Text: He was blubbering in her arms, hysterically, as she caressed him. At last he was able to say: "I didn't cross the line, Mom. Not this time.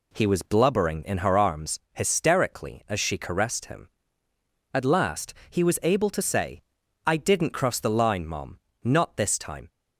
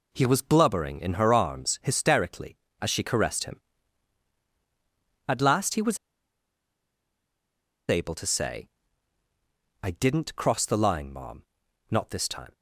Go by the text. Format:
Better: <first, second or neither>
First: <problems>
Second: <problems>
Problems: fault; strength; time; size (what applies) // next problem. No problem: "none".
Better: first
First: none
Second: pauses between "was" and "able"; strong; at 5.9 s; 1.9 s long